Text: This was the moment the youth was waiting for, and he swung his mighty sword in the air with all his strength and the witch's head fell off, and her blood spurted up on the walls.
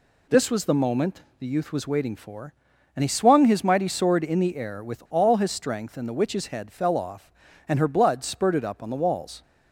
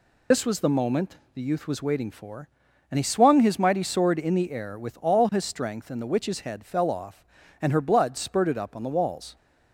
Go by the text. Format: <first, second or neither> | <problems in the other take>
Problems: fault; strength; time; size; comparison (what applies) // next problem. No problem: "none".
first | loses the start of "This"; at 0.3 s; 55 ms // pauses between "moment" and "the"; slight; at 1.1 s; 0.16 s long; slight in the first